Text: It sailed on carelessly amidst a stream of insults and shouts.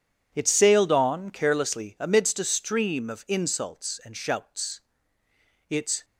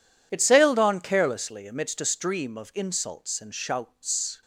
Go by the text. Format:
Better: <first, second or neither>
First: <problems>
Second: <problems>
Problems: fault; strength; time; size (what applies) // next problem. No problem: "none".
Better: second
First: goes on to say "Its"; slight; from 5.6 s on; 0.36 s long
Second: none